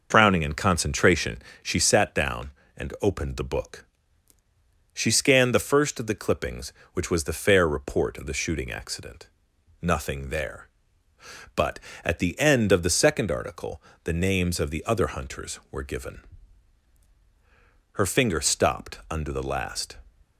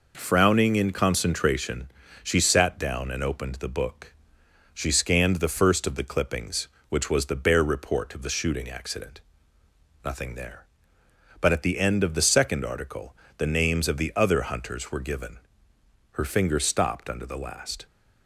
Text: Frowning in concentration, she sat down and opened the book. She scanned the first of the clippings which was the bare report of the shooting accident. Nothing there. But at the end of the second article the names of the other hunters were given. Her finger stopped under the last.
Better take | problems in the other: second | says "fair" for "bare"; at 7.3 s // pauses between "article" and "the"; slight; at 13.8 s; 0.22 s long; slight in the second

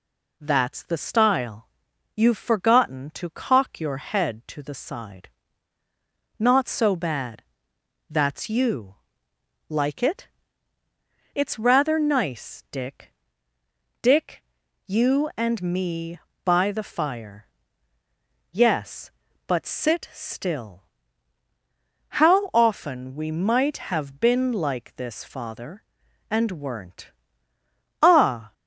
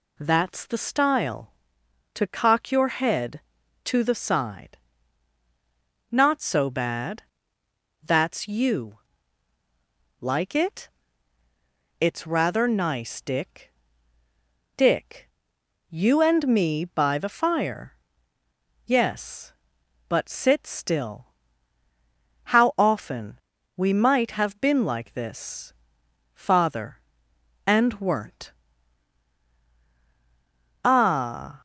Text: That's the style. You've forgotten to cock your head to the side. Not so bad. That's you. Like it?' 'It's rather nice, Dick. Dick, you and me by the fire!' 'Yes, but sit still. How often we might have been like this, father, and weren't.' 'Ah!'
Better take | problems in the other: first | skips "You've forgotten"; at 1.8 s // pauses between "often" and "we"; at 23.3 s; 0.38 s long

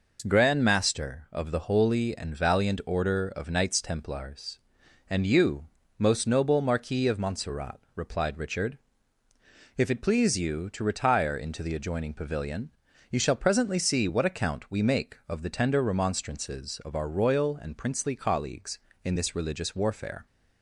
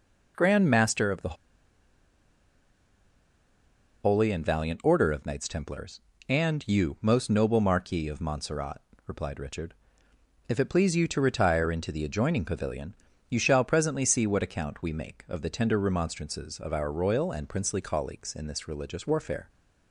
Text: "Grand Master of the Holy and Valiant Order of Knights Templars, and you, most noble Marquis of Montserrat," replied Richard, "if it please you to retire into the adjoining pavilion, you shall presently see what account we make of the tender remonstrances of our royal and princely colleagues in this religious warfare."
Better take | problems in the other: first | pauses between "the" and "Holy"; strong; at 1.3 s; 2.7 s long

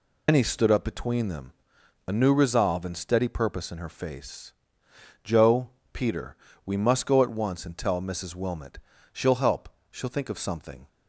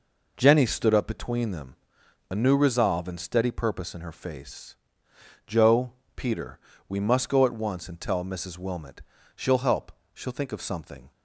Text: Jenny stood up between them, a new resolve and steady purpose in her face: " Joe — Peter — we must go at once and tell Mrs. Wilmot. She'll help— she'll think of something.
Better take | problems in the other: second | loses the start of "Jenny"; at 0.2 s; 150 ms

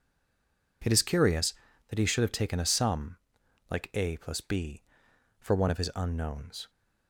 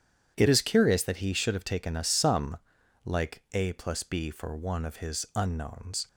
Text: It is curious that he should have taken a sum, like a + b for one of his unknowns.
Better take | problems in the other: second | stays silent before the first word; slight; until 0.8 s; 0.8 s long

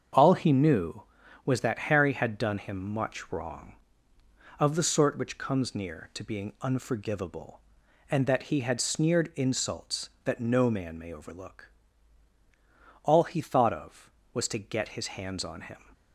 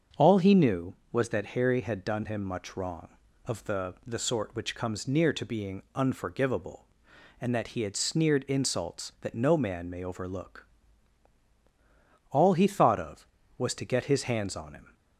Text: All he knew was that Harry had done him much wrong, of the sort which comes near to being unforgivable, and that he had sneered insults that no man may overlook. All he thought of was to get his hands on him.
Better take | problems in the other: first | starts louder than the rest; until 1.3 s; 6.5 dB; strong in the first // says "the" twice; at 4.0 s

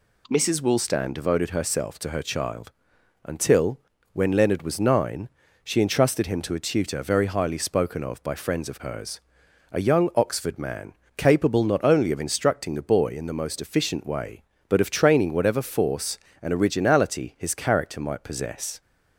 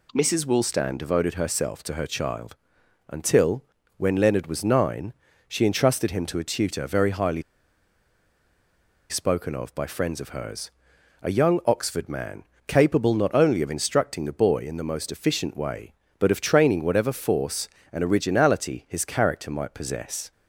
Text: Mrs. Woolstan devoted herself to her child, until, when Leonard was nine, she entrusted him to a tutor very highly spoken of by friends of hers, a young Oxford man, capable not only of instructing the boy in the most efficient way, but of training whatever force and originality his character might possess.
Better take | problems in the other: first | pauses between "highly" and "spoken"; strong; at 7.4 s; 1.6 s long

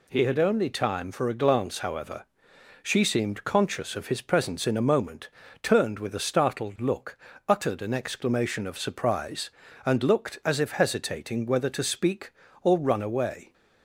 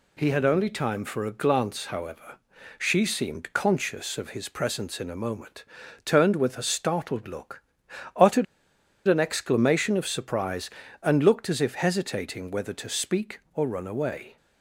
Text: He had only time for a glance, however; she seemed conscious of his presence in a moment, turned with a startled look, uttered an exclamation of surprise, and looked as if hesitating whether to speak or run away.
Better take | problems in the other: first | pauses between "uttered" and "an"; noticeable; at 8.4 s; 0.63 s long

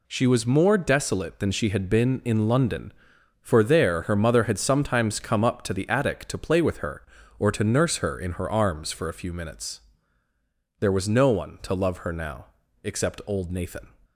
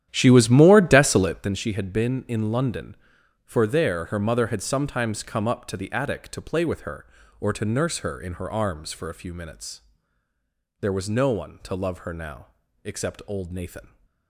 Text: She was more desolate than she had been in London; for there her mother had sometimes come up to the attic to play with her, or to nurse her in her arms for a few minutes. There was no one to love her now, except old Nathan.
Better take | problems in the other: first | starts louder than the rest; strong; until 1.5 s; 11 dB

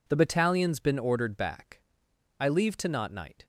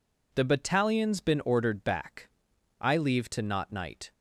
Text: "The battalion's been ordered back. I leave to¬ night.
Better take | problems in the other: neither | none

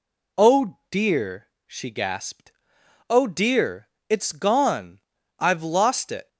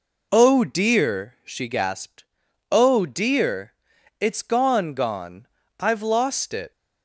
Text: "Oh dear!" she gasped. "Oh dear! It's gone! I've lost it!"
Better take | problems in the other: first | says "gone" twice; at 4.9 s

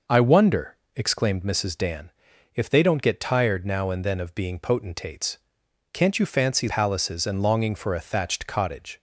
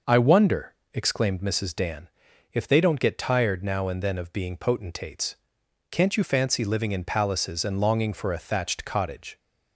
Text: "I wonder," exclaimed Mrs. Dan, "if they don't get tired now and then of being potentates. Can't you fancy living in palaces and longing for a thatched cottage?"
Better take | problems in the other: second | skips "living in"; at 6.6 s

